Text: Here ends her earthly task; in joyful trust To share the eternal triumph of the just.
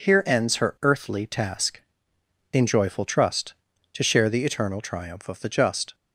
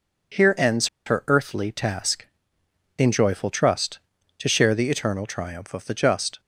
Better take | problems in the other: first | pauses between "ends" and "her"; slight; at 0.8 s; 0.19 s long

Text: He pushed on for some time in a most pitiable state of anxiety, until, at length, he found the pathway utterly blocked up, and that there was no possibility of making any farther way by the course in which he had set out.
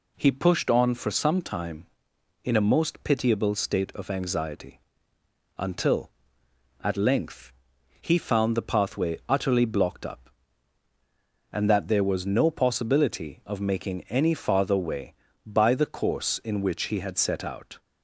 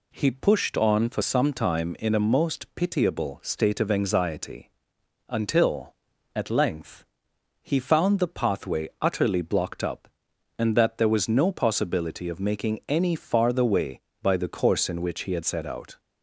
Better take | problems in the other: neither | none

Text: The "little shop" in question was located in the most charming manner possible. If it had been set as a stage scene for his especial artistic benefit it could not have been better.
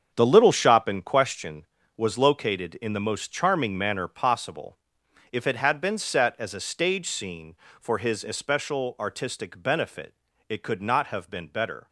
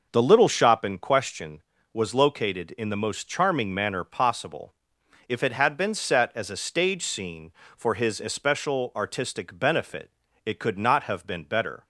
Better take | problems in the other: second | gets quieter; strong; throughout; 11 dB // pauses between "benefit" and "it"; slight; at 10.1 s; 0.34 s long; slight in the second

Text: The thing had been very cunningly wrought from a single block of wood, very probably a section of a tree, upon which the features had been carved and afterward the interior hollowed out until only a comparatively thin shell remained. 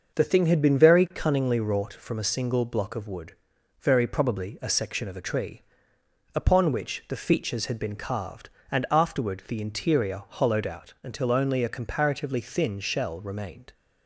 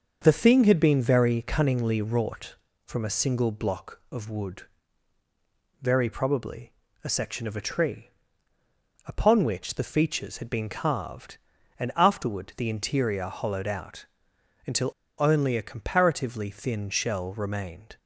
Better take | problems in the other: first | starts louder than the rest; until 1.2 s; 6.5 dB; noticeable in the first // pauses between "probably" and "a"; slight; at 6.7 s; 0.32 s long // pauses between "out" and "until"; noticeable; at 14.0 s; 0.60 s long // pauses between "until" and "only"; slight; at 14.9 s; 0.26 s long

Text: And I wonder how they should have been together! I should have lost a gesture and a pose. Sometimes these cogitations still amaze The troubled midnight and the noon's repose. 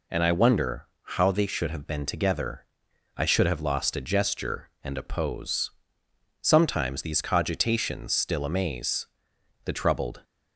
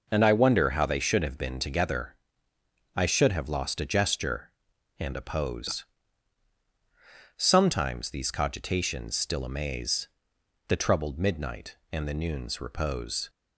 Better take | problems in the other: second | pauses between "wonder" and "how"; slight; at 0.8 s; 0.16 s long // pauses between "amaze" and "The"; noticeable; at 9.0 s; 0.58 s long; noticeable in the second // stops before "midnight and the noon's repose"; at 10.2 s

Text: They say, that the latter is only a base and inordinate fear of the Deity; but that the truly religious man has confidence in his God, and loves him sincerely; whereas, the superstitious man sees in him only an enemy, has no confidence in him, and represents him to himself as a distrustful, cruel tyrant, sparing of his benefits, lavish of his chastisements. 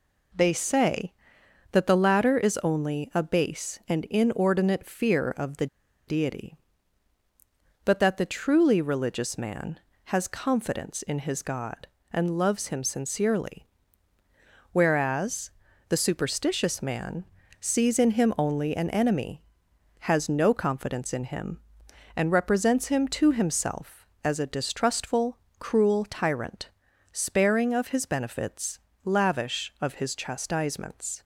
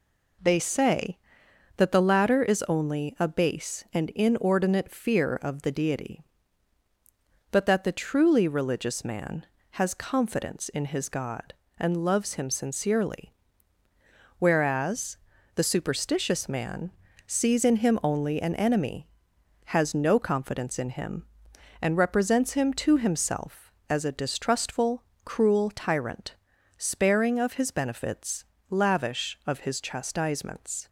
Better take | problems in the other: second | pauses between "the" and "Deity"; at 5.6 s; 0.41 s long // pauses between "man" and "sees"; slight; at 17.2 s; 0.36 s long; slight in the second

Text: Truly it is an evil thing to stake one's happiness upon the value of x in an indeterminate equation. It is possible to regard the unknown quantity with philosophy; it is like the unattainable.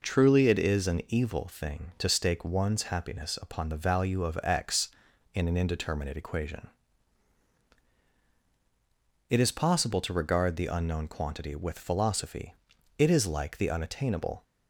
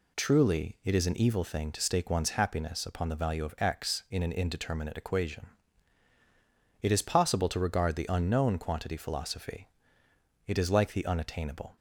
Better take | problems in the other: first | skips "with"; at 8.9 s

